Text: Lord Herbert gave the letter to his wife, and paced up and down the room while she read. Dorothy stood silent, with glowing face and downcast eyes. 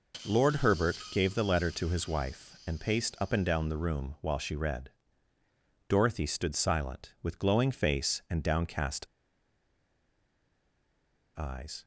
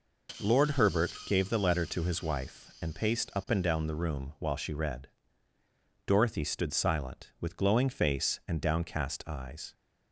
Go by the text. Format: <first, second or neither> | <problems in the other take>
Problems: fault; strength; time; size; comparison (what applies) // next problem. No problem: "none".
second | pauses between "Herbert" and "gave"; slight; at 0.9 s; 0.16 s long; slight in the second // pauses between "downcast" and "eyes"; strong; at 9.0 s; 2.3 s long